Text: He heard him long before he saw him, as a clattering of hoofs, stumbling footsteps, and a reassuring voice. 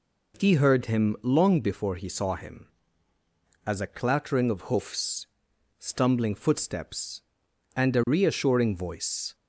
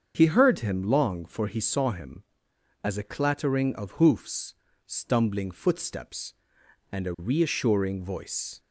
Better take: first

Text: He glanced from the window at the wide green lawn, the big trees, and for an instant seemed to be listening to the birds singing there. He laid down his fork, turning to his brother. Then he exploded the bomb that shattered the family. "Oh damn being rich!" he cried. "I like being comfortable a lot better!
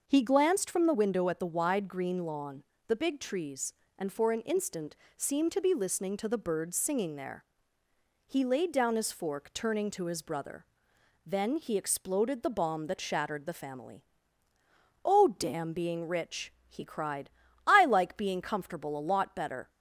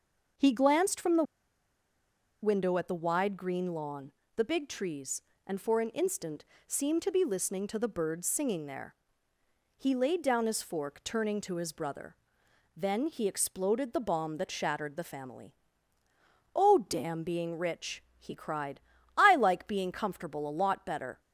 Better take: first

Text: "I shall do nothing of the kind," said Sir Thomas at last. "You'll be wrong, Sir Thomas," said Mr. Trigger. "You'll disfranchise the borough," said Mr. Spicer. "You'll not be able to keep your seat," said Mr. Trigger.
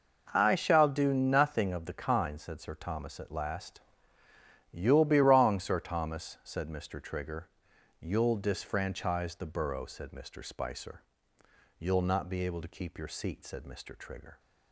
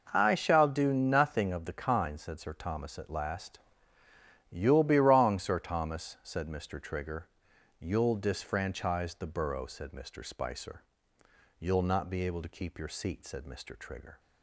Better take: neither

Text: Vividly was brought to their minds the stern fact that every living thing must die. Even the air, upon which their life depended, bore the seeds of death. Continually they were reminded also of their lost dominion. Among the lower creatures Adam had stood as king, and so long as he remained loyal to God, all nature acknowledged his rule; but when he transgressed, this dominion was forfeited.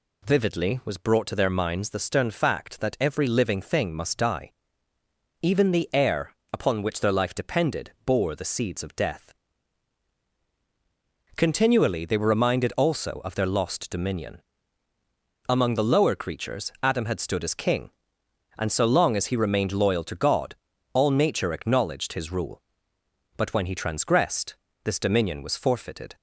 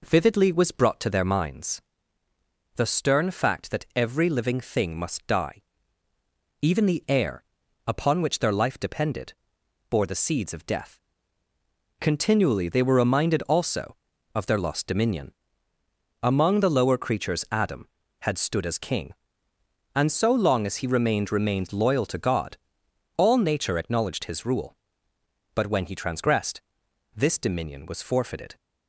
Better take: first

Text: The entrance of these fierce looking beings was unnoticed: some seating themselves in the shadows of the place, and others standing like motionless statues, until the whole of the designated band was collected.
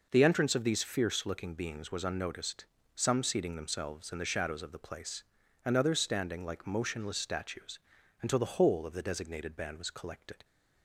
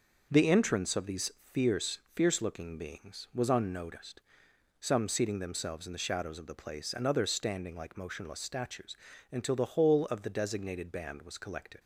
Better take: first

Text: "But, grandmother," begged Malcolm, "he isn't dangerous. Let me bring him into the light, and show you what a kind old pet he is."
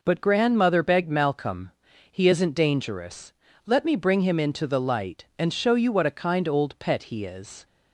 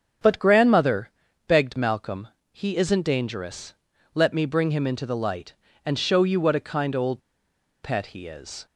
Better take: first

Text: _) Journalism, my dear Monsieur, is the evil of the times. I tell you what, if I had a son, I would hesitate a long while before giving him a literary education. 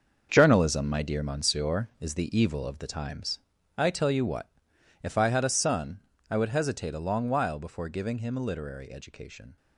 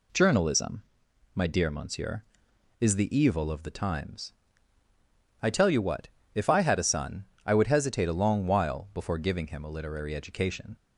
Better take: second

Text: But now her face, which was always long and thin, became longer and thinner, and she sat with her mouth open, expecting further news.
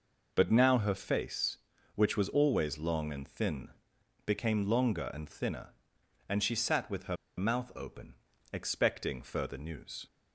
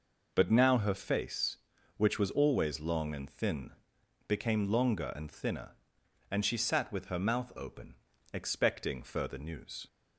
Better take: second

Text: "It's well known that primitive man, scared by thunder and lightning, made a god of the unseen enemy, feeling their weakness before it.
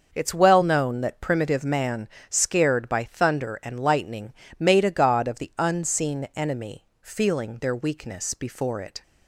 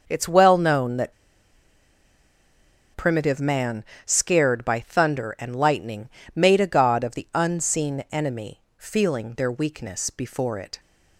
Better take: first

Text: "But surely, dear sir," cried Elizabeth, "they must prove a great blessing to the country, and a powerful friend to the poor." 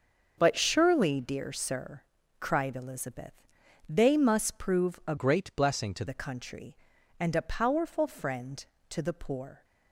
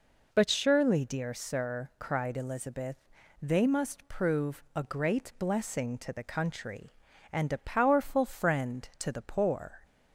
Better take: second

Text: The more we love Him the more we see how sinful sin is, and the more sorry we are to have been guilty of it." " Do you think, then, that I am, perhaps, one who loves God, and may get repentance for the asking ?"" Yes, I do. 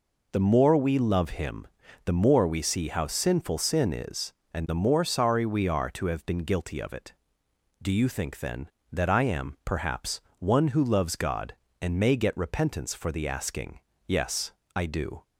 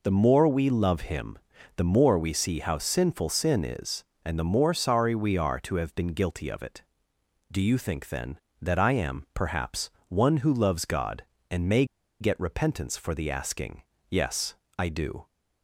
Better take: first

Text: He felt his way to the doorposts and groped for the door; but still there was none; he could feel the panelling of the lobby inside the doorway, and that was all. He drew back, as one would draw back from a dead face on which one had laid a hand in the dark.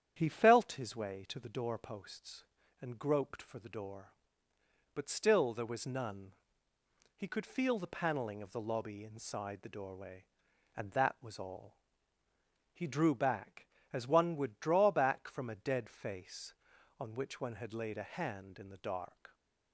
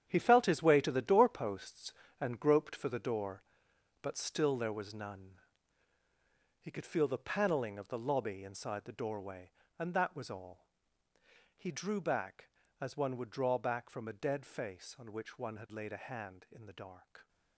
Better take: first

